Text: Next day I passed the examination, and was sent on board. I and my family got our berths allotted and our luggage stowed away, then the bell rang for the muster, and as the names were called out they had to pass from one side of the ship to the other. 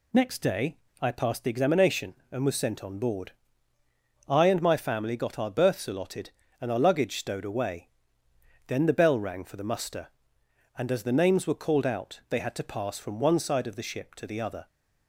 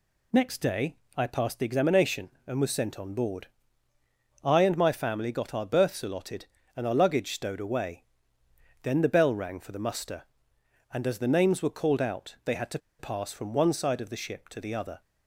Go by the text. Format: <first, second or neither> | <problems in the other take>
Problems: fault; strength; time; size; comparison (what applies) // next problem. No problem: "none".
first | pauses between "day" and "I"; slight; at 0.9 s; 0.22 s long; slight in the first // pauses between "to" and "pass"; slight; at 12.7 s; 0.20 s long